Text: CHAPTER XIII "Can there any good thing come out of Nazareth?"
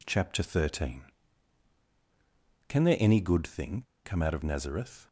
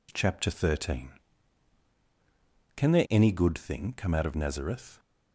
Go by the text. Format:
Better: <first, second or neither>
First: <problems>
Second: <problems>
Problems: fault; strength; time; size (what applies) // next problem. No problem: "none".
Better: second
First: pauses between "thing" and "come"; slight; at 3.8 s; 0.21 s long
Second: none